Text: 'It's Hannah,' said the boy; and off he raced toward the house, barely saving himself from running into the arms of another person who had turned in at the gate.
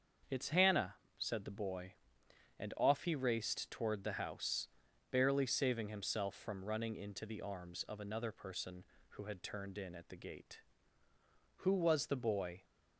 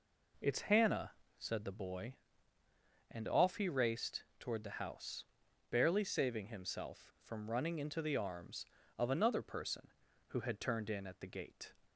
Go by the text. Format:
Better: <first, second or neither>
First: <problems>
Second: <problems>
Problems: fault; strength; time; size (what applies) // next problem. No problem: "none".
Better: second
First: starts louder than the rest; until 1.5 s; 6.5 dB // goes on to say "Who was the boy"; noticeable; from 11.5 s on; 1.0 s long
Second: none